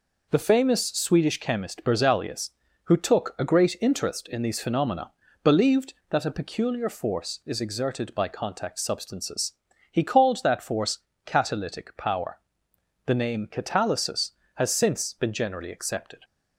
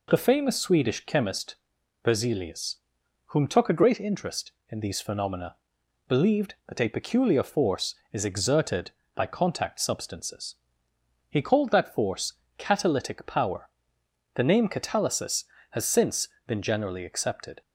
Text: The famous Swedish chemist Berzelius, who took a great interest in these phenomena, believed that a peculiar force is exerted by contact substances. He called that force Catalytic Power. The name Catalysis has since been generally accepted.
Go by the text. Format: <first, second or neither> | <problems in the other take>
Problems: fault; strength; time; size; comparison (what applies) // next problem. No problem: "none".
first | pauses between "chemist" and "Berzelius"; noticeable; at 1.5 s; 0.50 s long // says "whom" for "who"; at 3.2 s // pauses between "force" and "Catalytic"; slight; at 12.3 s; 0.24 s long; slight in the first // pauses between "since" and "been"; slight; at 16.2 s; 0.20 s long